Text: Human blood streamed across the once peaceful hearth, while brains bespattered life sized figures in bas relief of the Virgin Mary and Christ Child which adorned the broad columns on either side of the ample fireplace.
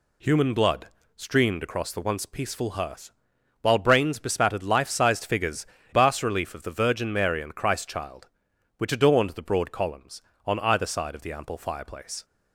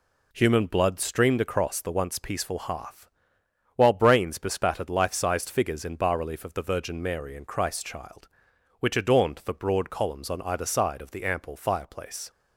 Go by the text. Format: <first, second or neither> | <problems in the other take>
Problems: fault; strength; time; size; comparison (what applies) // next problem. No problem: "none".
second | pauses between "blood" and "streamed"; slight; at 0.8 s; 0.30 s long // skips "in"; at 5.7 s